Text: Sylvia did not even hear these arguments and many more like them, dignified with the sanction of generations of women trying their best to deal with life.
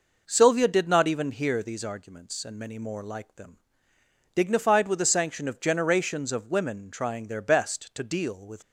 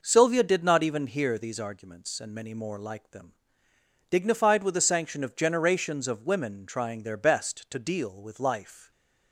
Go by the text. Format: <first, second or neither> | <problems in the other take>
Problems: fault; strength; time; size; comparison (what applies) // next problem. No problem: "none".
second | stops before "life"; at 8.6 s